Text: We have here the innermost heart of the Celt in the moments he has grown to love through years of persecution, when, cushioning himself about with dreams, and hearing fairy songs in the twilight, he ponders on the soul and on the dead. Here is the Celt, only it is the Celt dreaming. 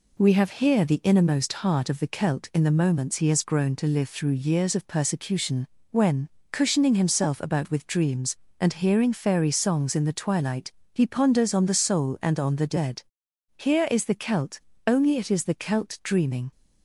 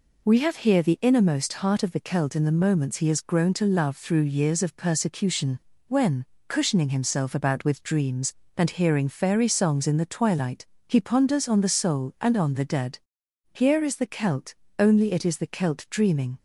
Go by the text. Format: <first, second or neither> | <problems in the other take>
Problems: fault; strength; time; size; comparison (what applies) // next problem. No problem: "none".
second | says "live" for "love"; at 3.8 s